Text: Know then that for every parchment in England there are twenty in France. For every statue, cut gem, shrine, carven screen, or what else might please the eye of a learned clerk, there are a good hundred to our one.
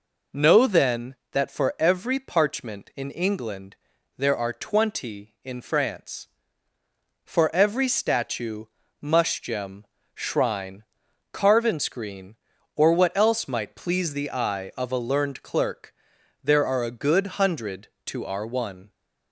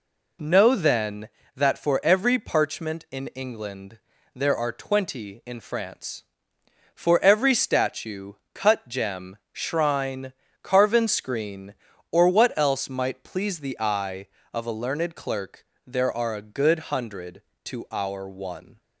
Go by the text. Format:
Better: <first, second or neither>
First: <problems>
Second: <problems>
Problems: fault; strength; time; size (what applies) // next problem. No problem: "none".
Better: second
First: pauses between "England" and "there"; at 3.7 s; 0.42 s long // says "mush" for "cut"; at 9.0 s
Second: pauses between "England" and "there"; slight; at 3.9 s; 0.36 s long